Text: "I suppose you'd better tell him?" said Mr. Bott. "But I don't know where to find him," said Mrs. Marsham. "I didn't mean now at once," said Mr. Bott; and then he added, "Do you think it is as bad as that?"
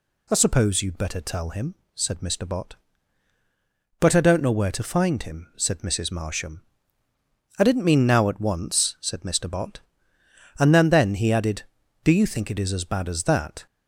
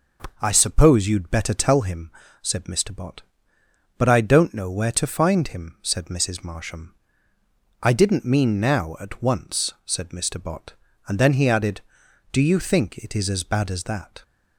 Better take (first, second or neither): second